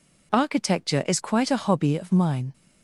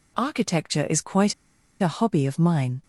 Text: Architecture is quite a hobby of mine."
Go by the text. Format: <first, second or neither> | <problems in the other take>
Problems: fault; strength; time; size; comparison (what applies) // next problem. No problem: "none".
first | pauses between "quite" and "a"; noticeable; at 1.3 s; 0.46 s long